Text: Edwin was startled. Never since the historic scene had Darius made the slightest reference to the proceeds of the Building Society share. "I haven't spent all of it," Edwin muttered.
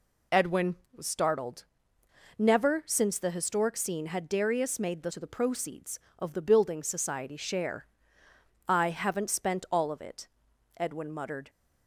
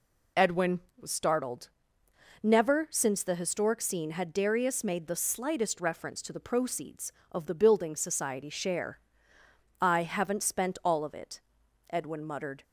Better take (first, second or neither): second